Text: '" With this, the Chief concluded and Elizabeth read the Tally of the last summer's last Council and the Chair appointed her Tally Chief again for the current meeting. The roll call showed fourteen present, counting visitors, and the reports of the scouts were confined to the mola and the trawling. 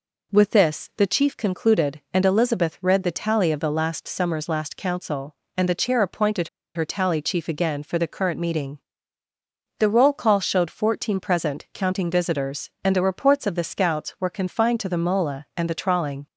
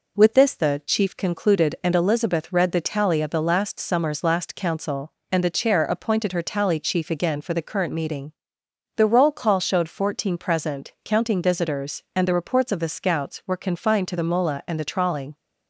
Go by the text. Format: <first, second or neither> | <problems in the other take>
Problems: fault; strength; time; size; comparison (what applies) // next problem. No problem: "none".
second | pauses between "appointed" and "her"; slight; at 6.4 s; 0.26 s long